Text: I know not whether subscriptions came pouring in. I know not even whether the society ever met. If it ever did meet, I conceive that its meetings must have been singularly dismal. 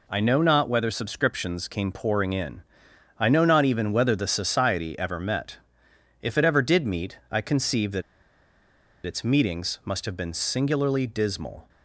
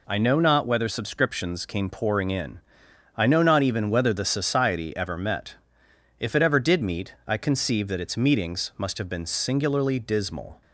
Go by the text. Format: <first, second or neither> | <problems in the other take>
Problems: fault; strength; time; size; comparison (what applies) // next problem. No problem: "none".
second | pauses between "that" and "its"; at 8.0 s; 1.0 s long